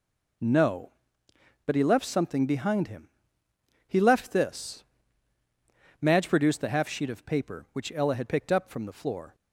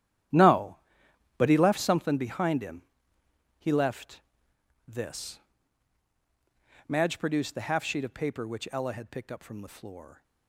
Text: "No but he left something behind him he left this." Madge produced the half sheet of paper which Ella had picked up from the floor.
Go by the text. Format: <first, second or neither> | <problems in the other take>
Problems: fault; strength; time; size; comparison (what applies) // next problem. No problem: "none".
first | gets quieter; strong; throughout; 14 dB // pauses between "him" and "he"; noticeable; at 2.8 s; 0.76 s long; noticeable in the first // pauses between "left" and "this"; noticeable; at 4.2 s; 0.66 s long